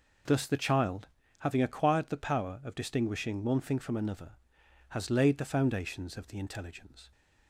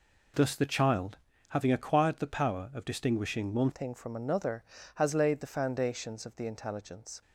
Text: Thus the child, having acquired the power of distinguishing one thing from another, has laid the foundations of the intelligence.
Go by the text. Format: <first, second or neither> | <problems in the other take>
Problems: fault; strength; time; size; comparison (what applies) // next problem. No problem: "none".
first | changes voice at "thing"; from 3.7 s on; 3.5 s long